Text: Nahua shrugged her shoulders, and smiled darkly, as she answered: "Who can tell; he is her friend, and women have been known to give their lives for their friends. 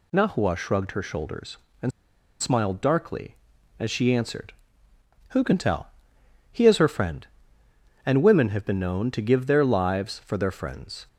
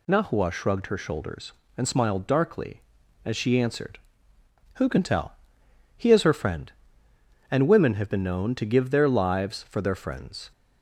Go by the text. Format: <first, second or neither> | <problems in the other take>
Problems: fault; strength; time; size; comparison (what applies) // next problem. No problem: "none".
second | pauses between "and" and "smiled"; noticeable; at 1.9 s; 0.50 s long